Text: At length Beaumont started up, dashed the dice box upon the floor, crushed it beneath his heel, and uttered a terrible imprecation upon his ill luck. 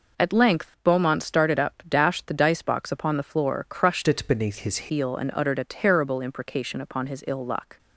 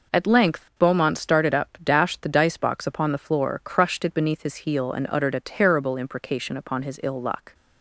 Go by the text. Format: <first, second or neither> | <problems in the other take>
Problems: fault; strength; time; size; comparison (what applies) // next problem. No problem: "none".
second | changes voice from "it" to "his"; from 4.0 to 4.7 s; 0.7 s long